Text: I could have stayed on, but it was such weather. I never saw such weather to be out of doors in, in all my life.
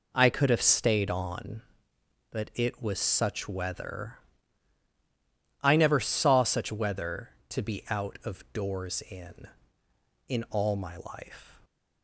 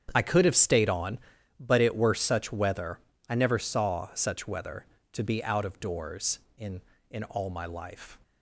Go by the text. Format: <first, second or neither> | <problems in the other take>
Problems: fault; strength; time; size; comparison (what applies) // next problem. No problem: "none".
first | starts louder than the rest; strong; until 1.1 s; 8.5 dB // says "were" for "was"; at 1.9 s